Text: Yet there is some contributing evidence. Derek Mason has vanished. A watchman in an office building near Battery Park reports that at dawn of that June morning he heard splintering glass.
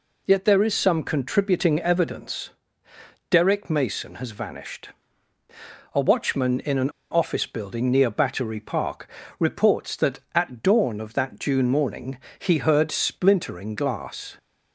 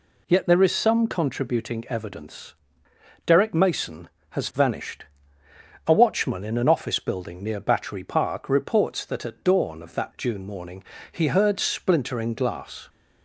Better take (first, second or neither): second